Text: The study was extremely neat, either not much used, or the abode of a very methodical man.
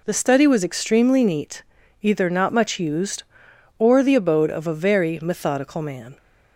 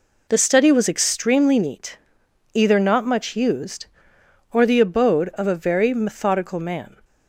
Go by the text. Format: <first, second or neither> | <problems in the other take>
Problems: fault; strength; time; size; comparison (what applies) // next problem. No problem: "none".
neither | none